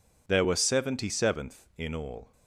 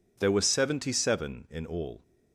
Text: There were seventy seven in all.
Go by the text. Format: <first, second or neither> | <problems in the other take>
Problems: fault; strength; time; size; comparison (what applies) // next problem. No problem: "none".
second | says "seventh" for "seven"; at 1.0 s